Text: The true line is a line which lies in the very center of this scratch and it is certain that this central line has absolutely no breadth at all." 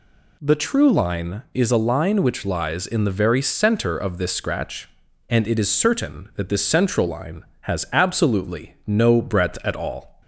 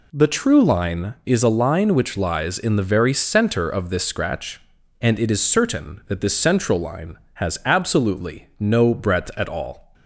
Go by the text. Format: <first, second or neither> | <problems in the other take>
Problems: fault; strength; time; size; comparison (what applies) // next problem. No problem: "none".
first | gets quieter; strong; throughout; 10 dB